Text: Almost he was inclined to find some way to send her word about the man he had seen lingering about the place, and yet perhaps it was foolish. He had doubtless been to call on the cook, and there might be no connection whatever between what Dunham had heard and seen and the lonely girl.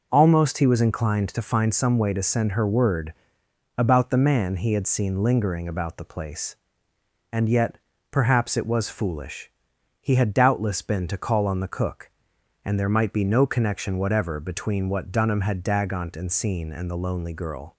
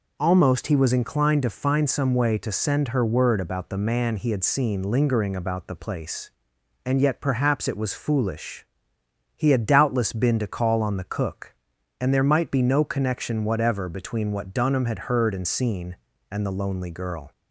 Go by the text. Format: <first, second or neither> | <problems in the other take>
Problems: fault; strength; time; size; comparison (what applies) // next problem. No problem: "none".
second | pauses between "word" and "about"; noticeable; at 3.1 s; 0.64 s long // pauses between "yet" and "perhaps"; slight; at 7.7 s; 0.32 s long // says "dagont" for "heard"; at 15.6 s